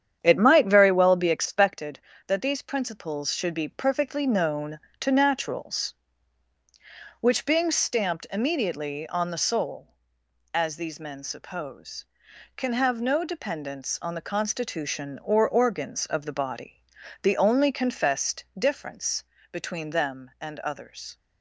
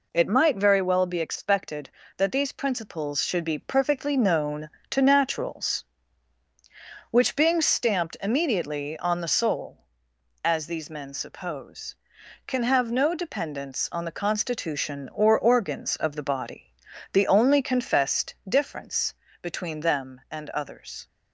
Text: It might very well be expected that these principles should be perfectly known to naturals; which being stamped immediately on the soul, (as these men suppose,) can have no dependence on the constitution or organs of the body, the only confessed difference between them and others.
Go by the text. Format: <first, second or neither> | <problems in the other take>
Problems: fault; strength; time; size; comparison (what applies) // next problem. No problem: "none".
second | starts louder than the rest; strong; until 1.7 s; 9 dB // pauses between "confessed" and "difference"; slight; at 18.4 s; 0.16 s long; slight in the second // pauses between "difference" and "between"; slight; at 19.2 s; 0.30 s long; slight in the second